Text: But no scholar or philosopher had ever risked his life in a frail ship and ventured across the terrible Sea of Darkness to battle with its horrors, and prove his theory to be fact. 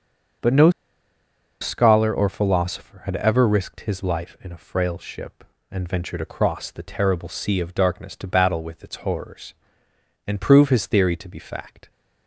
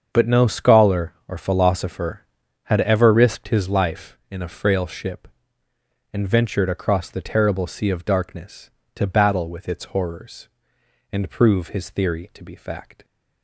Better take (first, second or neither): second